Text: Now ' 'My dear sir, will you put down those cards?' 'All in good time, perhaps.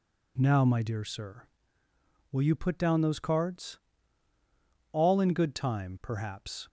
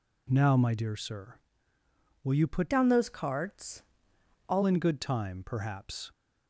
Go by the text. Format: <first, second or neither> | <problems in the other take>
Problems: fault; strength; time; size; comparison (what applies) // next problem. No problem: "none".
first | changes voice from "down" to "All"; from 2.7 to 4.6 s; 1.9 s long